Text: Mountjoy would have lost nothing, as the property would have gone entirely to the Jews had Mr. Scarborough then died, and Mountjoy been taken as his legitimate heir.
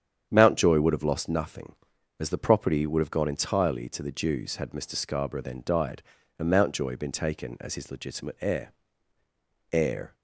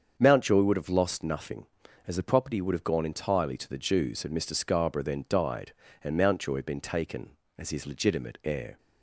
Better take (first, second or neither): second